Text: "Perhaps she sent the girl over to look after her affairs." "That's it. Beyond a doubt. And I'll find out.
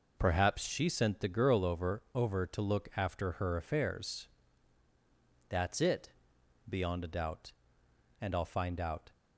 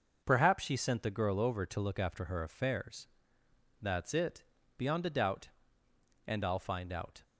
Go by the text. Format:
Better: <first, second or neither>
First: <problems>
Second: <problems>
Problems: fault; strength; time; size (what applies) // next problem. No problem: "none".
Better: second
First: says "over" twice; at 2.1 s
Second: none